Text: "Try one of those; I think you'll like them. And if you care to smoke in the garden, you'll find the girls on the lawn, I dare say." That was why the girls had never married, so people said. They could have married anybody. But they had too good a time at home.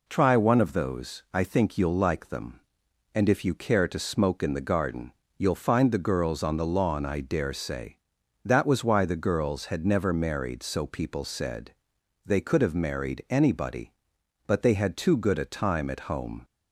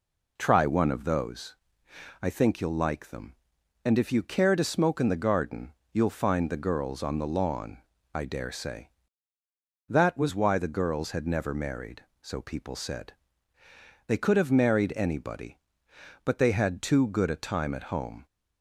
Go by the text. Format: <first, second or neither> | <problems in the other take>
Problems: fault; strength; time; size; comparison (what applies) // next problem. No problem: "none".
neither | none